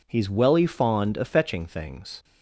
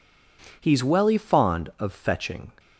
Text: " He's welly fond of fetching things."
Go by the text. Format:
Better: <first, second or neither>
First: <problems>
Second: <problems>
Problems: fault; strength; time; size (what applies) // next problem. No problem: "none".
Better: first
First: none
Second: stops before "things"; at 2.5 s